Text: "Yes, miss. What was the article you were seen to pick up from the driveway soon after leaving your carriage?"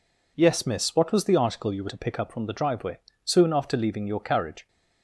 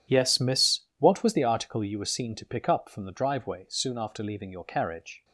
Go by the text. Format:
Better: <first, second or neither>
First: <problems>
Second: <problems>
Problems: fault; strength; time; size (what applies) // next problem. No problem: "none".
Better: second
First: skips "seen"; at 1.8 s // pauses between "driveway" and "soon"; slight; at 2.9 s; 0.26 s long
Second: none